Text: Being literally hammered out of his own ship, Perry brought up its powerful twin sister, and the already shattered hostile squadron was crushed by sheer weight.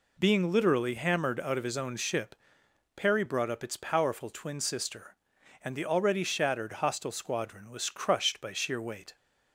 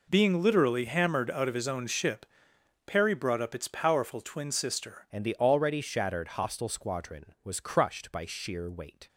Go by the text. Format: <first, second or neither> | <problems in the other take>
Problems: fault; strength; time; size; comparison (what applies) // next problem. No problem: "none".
first | changes voice at "and"; from 5.0 s on; 4.0 s long